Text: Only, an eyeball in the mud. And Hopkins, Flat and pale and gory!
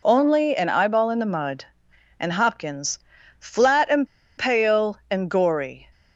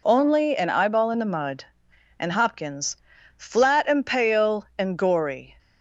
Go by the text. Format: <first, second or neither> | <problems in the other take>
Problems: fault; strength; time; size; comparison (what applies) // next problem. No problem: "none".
second | pauses between "and" and "pale"; slight; at 4.0 s; 0.32 s long